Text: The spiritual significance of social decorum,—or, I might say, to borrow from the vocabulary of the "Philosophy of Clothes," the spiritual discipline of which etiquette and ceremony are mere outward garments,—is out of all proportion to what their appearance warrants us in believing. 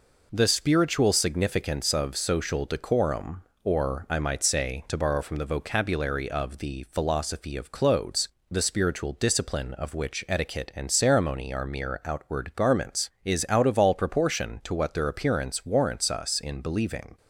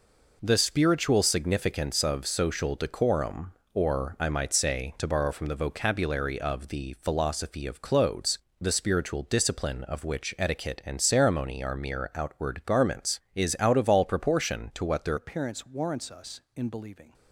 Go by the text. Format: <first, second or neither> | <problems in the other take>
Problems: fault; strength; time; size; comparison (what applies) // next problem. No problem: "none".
first | changes voice at "appearance"; from 15.1 s on; 2.0 s long